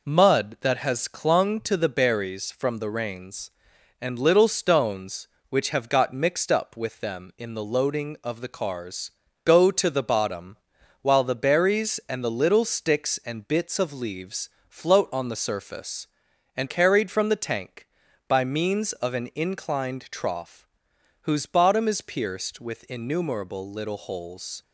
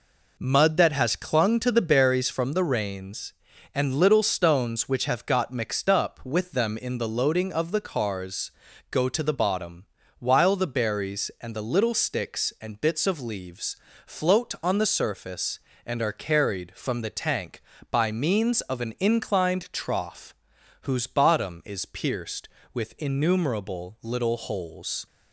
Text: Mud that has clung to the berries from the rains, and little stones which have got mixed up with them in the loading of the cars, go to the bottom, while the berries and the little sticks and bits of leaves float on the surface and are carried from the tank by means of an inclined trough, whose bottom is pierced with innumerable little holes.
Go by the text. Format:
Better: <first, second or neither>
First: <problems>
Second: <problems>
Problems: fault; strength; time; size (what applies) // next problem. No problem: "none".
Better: second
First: pauses between "leaves" and "float"; slight; at 14.4 s; 0.22 s long // skips "are"; at 16.6 s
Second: pauses between "leaves" and "float"; slight; at 13.7 s; 0.32 s long